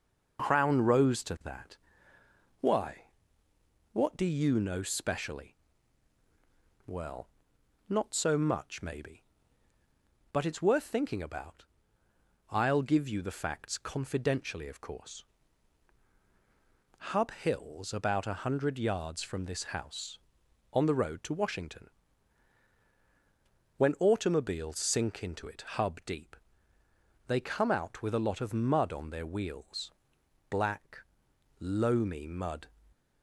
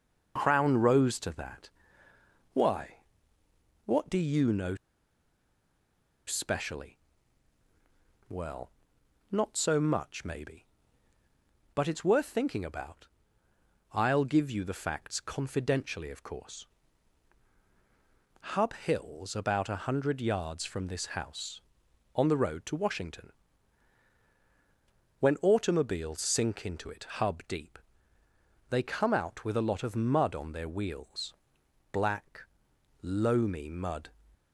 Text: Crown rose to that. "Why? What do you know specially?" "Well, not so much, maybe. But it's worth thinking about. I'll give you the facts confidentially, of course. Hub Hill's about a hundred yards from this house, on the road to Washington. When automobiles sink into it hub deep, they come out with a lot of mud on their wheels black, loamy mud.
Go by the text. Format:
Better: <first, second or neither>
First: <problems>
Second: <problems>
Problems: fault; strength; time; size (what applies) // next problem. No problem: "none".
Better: first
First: pauses between "wheels" and "black"; noticeable; at 29.8 s; 0.60 s long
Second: pauses between "know" and "specially"; strong; at 4.7 s; 1.5 s long // pauses between "wheels" and "black"; noticeable; at 31.3 s; 0.60 s long